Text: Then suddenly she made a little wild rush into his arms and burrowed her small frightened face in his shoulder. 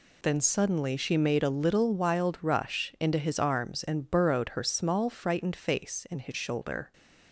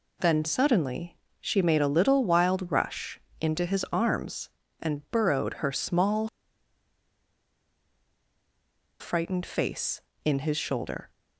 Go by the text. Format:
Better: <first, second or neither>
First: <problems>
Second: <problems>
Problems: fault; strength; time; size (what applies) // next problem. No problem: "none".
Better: first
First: none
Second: pauses between "suddenly" and "she"; slight; at 1.1 s; 0.24 s long // pauses between "rush" and "into"; slight; at 3.1 s; 0.22 s long // pauses between "small" and "frightened"; strong; at 6.2 s; 2.7 s long